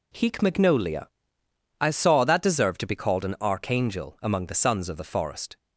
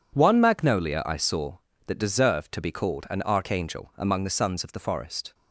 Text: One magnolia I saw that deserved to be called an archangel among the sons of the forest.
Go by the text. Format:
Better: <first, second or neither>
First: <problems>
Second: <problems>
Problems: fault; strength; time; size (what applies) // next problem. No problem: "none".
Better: second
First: says "Heek" for "One"; at 0.1 s // pauses between "magnolia" and "I"; noticeable; at 1.0 s; 0.74 s long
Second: none